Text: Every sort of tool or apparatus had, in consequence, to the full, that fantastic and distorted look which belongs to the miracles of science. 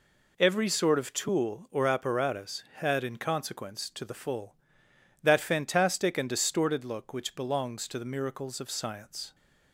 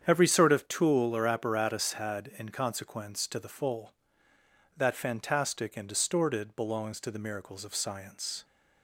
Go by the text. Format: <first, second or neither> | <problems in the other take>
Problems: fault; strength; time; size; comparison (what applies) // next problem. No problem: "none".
first | starts louder than the rest; strong; until 1.0 s; 8 dB // skips "look which"; at 6.5 s